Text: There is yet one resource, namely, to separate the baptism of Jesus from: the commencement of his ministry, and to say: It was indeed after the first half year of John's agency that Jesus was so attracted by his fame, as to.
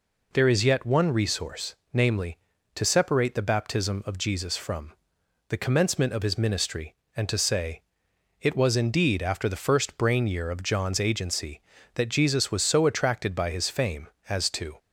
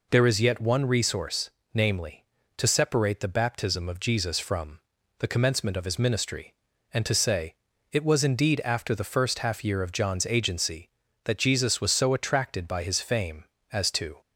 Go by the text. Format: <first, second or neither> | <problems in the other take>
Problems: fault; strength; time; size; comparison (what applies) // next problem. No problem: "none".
second | says "brain" for "half"; at 9.9 s